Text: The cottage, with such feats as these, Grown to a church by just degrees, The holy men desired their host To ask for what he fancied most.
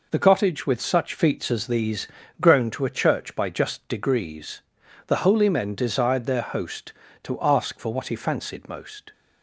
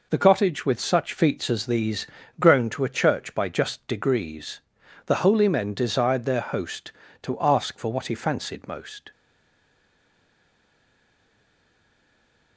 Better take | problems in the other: first | stays silent after the last word; strong; from 9.1 s on; 3.4 s long

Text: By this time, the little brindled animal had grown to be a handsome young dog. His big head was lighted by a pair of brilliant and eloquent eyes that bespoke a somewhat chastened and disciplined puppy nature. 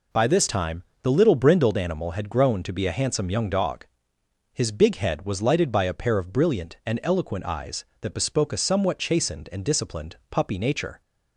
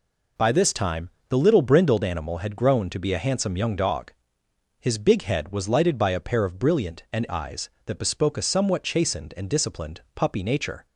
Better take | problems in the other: first | skips "eloquent"; at 7.2 s

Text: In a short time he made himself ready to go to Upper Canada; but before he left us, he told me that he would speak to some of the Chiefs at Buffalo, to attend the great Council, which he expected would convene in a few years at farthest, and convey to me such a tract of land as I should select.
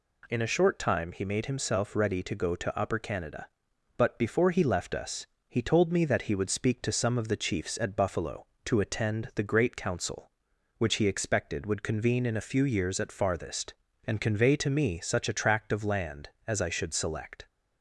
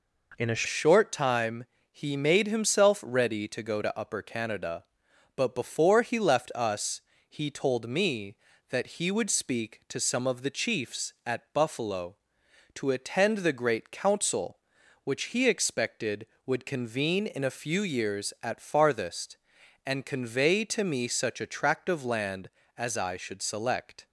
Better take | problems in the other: first | changes voice at "short"; from 0.6 s on; 23.4 s long // pauses between "time" and "he"; slight; at 1.6 s; 0.26 s long

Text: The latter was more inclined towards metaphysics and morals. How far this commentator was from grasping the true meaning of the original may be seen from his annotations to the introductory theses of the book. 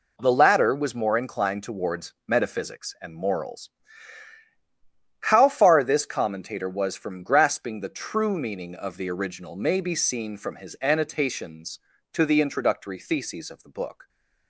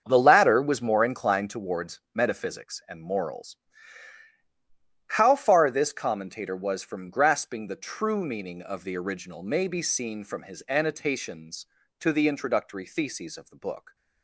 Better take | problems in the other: first | starts louder than the rest; until 1.6 s; 7 dB

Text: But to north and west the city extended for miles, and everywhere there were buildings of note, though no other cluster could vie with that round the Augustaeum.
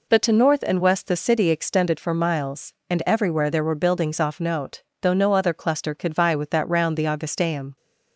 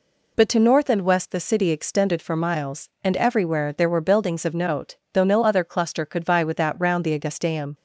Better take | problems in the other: second | says "off" for "of"; at 4.1 s

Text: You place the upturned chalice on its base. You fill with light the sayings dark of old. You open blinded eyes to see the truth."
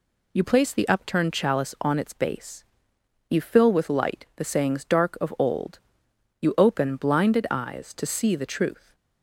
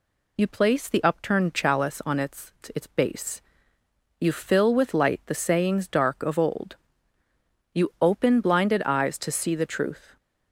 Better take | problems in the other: first | says "its" twice; at 2.7 s

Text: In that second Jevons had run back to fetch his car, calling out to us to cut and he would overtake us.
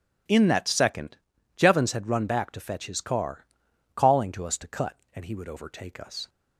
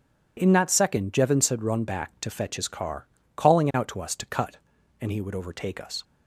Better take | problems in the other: second | pauses between "second" and "Jevons"; at 1.1 s; 0.38 s long // skips "out"; at 4.3 s

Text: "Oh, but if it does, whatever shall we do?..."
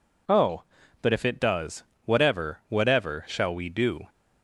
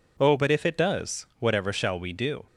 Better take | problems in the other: second | says "whatever" twice; at 2.6 s

